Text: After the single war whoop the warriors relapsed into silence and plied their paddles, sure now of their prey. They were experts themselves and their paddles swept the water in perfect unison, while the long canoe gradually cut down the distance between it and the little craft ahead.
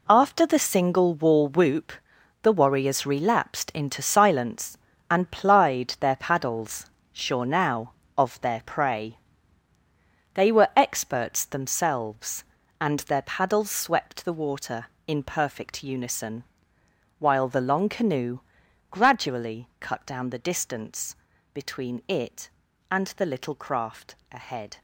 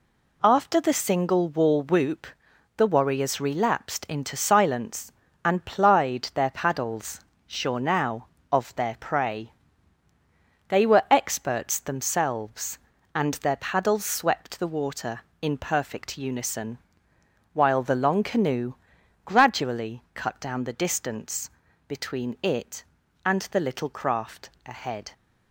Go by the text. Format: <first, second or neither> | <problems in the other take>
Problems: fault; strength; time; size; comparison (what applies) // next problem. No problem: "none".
second | gets quieter; strong; throughout; 10.5 dB // pauses between "whoop" and "the"; noticeable; at 1.9 s; 0.52 s long; noticeable in the second // pauses between "canoe" and "gradually"; noticeable; at 18.3 s; 0.52 s long; noticeable in the second // pauses between "distance" and "between"; slight; at 21.1 s; 0.36 s long; slight in the second // pauses between "craft" and "ahead"; slight; at 24.1 s; 0.16 s long; slight in the second